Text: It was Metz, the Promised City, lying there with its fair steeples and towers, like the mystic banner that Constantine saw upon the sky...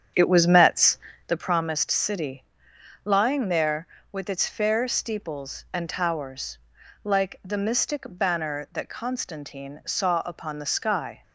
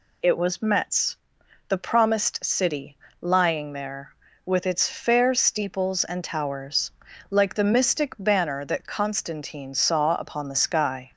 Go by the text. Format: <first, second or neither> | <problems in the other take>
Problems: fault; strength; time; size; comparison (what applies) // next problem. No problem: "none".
second | starts louder than the rest; strong; until 1.4 s; 8.5 dB